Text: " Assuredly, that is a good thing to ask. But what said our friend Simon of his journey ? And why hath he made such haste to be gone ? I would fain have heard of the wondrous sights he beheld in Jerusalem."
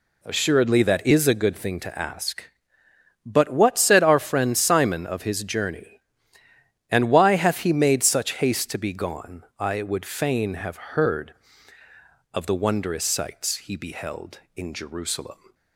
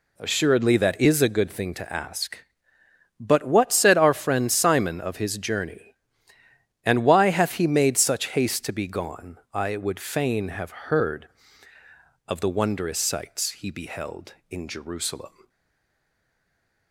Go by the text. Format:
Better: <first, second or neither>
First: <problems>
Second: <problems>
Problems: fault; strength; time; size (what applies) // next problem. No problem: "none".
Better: first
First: none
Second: stays silent after the last word; noticeable; from 15.4 s on; 1.5 s long